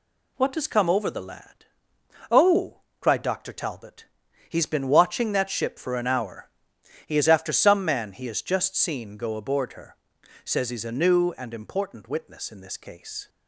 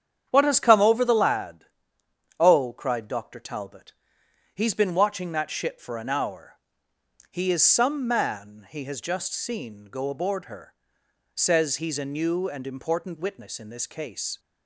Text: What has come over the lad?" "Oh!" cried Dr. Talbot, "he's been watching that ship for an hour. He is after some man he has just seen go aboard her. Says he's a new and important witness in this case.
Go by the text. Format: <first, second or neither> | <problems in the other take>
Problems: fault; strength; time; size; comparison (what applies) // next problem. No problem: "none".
first | starts louder than the rest; strong; until 1.3 s; 8.5 dB // skips "after"; at 7.6 s